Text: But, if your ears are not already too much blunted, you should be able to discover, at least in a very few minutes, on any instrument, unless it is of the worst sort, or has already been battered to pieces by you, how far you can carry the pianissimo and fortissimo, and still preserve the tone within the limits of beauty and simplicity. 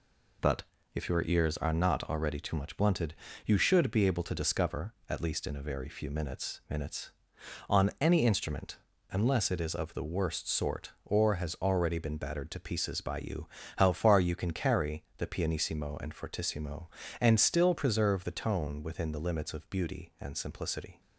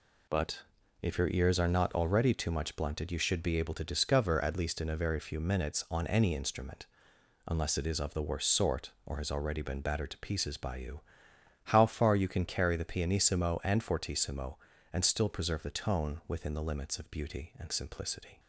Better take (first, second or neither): second